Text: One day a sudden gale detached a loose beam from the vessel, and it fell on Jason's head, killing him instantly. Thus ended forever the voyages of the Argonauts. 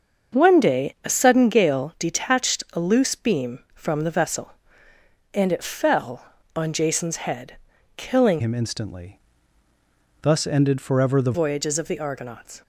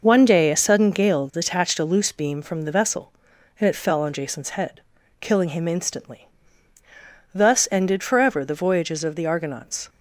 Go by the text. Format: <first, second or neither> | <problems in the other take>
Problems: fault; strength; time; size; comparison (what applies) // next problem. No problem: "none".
second | starts louder than the rest; until 1.4 s; 6.5 dB // changes voice from "him" to "the"; from 8.3 to 11.3 s; 3.0 s long